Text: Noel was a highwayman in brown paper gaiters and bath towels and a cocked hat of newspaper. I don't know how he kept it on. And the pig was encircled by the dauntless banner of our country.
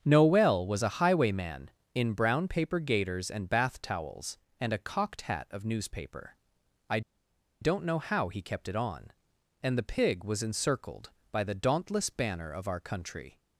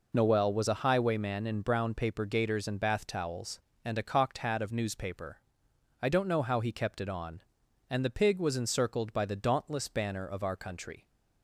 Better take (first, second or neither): second